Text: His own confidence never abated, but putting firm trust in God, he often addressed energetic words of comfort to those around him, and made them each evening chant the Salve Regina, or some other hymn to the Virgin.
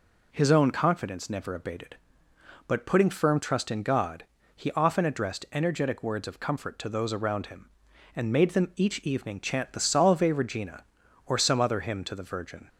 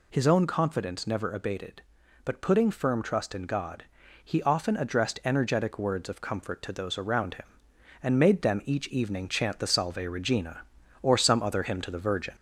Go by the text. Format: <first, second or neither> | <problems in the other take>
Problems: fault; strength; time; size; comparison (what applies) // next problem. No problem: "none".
first | gets louder; slight; throughout; 2 dB